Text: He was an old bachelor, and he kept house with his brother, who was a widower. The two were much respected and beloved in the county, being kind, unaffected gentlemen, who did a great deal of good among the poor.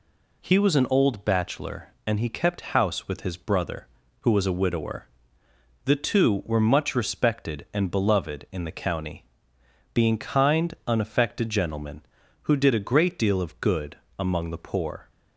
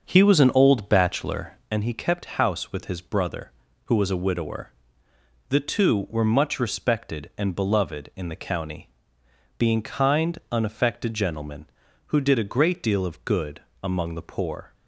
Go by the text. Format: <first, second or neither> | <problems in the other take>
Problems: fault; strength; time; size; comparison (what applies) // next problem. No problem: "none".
first | starts louder than the rest; until 1.7 s; 6.5 dB // pauses between "good" and "among"; slight; at 13.6 s; 0.20 s long; slight in the first